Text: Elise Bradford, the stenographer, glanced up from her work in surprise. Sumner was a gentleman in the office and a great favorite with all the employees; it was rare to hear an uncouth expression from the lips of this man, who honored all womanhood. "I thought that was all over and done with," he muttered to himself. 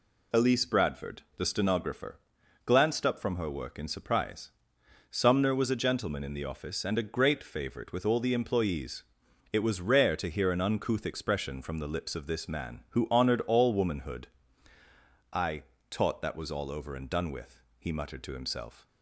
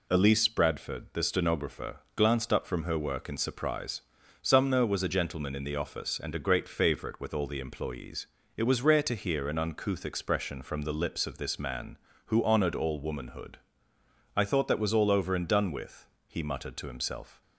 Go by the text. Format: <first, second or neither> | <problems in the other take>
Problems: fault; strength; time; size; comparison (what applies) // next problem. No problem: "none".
second | says "taught" for "thought"; at 15.8 s